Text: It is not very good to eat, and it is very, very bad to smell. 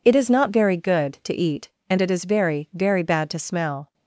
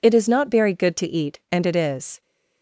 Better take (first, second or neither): first